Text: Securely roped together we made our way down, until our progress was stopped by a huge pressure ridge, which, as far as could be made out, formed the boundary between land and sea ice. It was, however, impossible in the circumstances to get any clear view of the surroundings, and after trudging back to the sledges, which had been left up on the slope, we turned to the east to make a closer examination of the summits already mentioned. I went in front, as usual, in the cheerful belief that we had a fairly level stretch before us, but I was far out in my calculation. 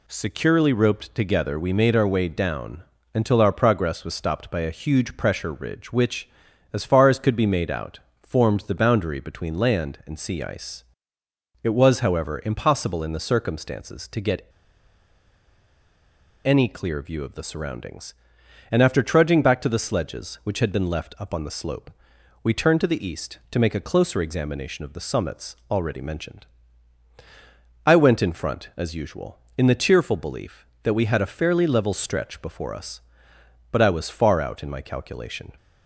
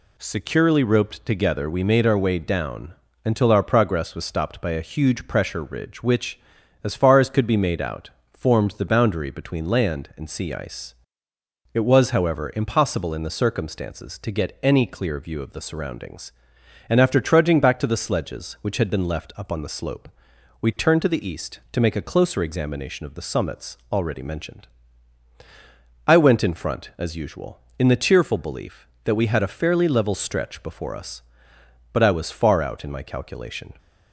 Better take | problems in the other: second | pauses between "get" and "any"; strong; at 14.4 s; 1.9 s long

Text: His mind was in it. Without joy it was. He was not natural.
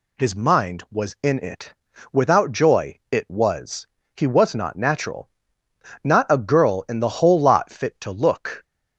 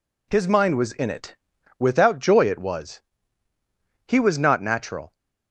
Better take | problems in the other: second | goes on to say "Not a girl in the whole lot fit to look"; strong; from 6.0 s on; 2.5 s long

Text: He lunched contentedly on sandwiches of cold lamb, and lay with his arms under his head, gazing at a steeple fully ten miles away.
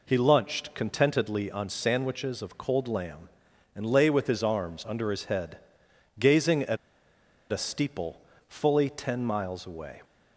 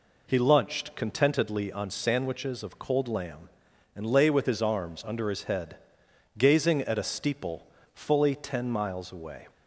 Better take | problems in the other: second | pauses between "at" and "a"; noticeable; at 6.7 s; 0.74 s long // pauses between "steeple" and "fully"; slight; at 8.2 s; 0.26 s long; slight in the second

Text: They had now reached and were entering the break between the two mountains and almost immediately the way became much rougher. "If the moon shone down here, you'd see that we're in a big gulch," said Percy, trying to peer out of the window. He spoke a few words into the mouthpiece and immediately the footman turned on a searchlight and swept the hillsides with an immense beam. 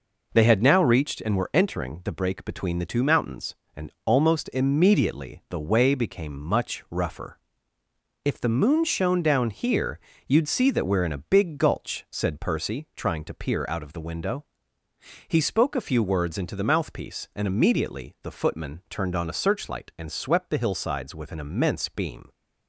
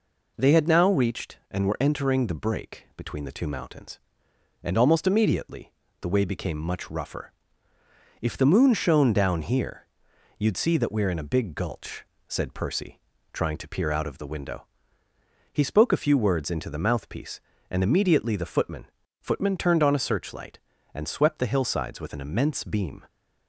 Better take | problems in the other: first | pauses between "immediately" and "the"; slight; at 5.7 s; 0.28 s long // says "footman" twice; at 19.2 s

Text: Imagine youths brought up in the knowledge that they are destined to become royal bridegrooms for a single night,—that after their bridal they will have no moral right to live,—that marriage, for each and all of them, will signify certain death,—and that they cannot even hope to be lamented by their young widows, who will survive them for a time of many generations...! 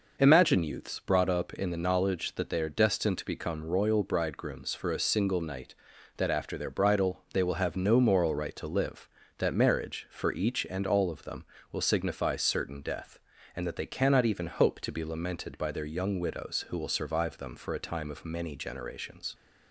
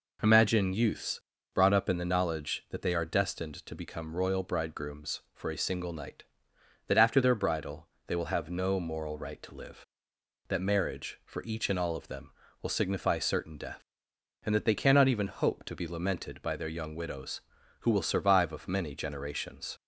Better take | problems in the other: first | pauses between "youths" and "brought"; slight; at 1.2 s; 0.34 s long // pauses between "bridal" and "they"; slight; at 7.8 s; 0.20 s long // skips "them for a time"; at 18.5 s

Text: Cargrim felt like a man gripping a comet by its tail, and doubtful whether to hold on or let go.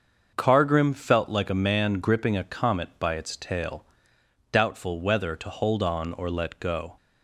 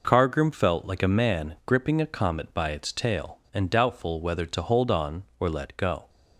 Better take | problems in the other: second | starts louder than the rest; until 1.3 s; 6.5 dB // skips "and"; at 4.1 s

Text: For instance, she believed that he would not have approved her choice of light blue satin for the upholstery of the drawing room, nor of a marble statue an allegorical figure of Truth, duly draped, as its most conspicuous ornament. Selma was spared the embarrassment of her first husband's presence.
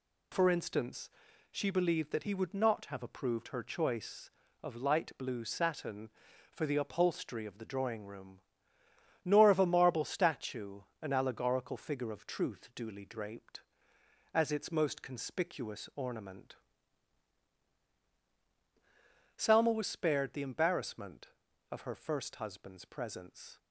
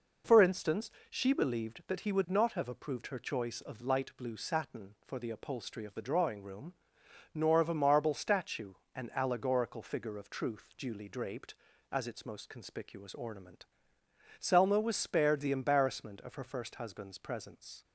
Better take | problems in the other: neither | pauses between "statue" and "an"; slight; the same in both

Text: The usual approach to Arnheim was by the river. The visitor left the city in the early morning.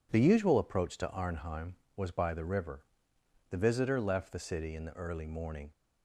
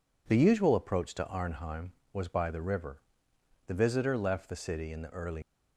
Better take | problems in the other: first | stops before "morning"; at 5.4 s

